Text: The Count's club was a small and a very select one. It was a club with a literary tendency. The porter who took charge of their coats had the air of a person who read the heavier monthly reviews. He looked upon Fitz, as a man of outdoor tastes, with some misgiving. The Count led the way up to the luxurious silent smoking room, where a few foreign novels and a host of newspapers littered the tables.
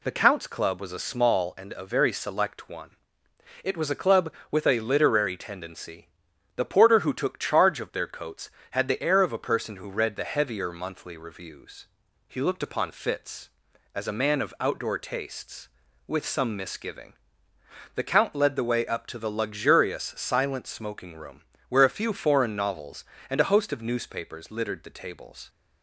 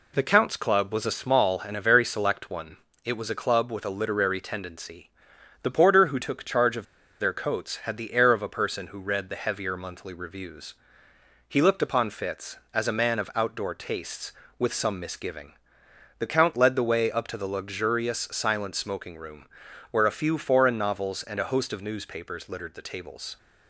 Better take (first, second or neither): first